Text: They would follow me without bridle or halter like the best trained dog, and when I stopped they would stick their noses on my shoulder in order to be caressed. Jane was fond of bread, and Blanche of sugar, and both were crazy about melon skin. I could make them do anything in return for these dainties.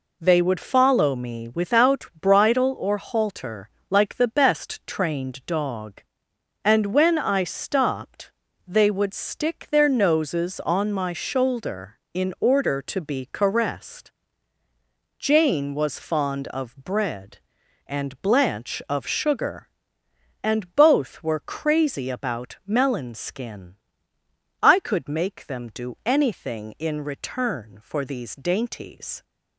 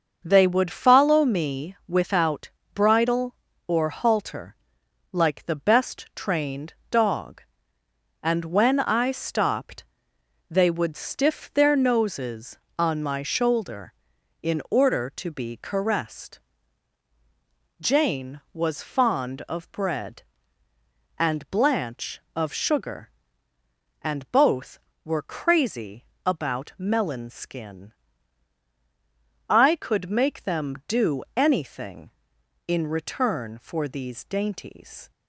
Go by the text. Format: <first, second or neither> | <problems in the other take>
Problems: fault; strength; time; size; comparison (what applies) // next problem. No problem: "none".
first | starts louder than the rest; until 1.2 s; 6 dB // pauses between "without" and "bridle"; slight; at 2.5 s; 0.24 s long // pauses between "halter" and "like"; noticeable; at 4.5 s; 0.58 s long; slight in the first // pauses between "trained" and "dog"; slight; at 6.7 s; 0.18 s long // pauses between "stopped" and "they"; noticeable; at 9.8 s; 0.66 s long; slight in the first // says "stiff" for "stick"; at 10.9 s // pauses between "crazy" and "about"; slight; at 26.0 s; 0.20 s long